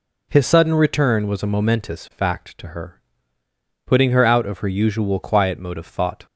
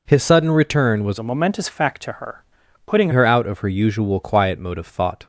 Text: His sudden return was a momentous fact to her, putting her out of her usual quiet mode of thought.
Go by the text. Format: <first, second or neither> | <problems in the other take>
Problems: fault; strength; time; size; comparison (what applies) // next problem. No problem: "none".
first | changes voice from "a" to "putting"; from 1.1 to 3.0 s; 1.9 s long